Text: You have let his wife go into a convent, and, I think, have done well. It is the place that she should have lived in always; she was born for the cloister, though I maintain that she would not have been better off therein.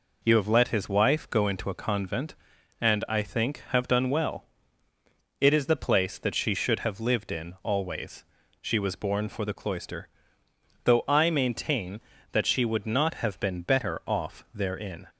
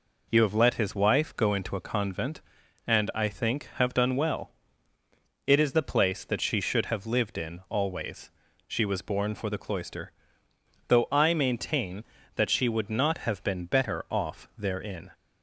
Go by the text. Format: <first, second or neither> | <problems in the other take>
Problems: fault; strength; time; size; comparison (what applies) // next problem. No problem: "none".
neither | none